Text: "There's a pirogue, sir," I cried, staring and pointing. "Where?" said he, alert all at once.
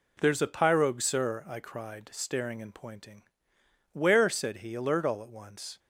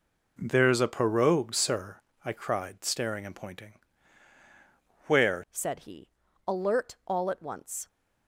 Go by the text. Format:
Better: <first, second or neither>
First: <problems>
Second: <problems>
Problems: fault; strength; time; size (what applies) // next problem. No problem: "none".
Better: first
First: none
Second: changes voice at "said"; from 5.5 s on; 2.3 s long